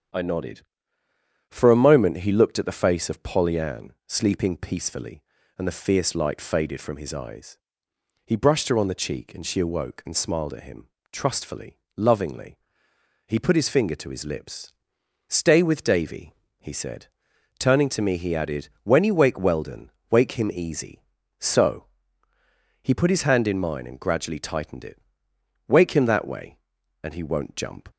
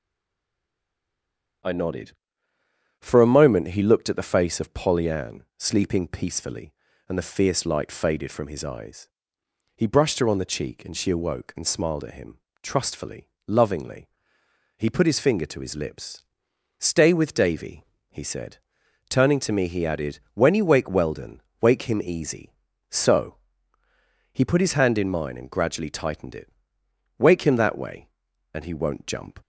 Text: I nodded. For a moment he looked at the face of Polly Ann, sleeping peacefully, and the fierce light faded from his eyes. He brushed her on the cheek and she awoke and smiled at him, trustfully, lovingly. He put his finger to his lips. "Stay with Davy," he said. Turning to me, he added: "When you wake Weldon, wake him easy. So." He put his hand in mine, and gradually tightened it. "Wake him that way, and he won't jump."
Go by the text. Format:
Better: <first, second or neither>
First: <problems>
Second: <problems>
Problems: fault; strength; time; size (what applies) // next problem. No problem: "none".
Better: first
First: starts louder than the rest; strong; until 2.0 s; 8 dB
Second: stays silent before the first word; noticeable; until 1.6 s; 1.6 s long // starts louder than the rest; strong; until 3.5 s; 8 dB